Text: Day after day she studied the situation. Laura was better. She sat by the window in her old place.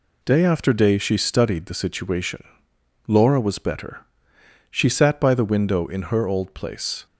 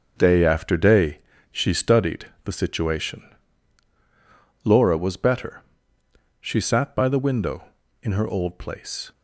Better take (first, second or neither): first